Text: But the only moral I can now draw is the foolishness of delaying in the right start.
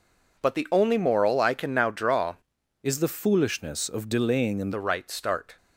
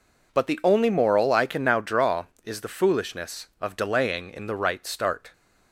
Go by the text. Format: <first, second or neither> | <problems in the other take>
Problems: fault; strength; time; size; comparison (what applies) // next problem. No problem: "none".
second | changes voice from "is" to "in"; from 2.8 to 4.7 s; 1.9 s long